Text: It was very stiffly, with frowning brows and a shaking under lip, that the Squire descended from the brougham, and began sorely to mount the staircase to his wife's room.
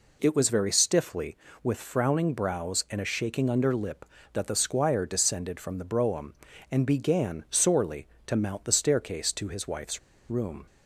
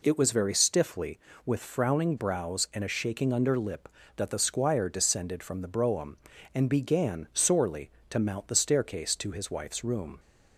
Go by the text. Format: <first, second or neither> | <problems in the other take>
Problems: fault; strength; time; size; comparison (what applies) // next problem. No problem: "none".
second | pauses between "wife's" and "room"; slight; at 9.9 s; 0.30 s long